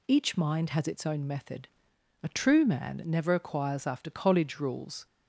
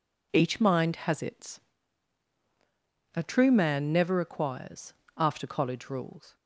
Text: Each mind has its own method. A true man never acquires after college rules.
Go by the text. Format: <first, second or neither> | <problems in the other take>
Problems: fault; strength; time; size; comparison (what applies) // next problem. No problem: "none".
first | skips "own method"; at 2.3 s // pauses between "acquires" and "after"; slight; at 4.9 s; 0.24 s long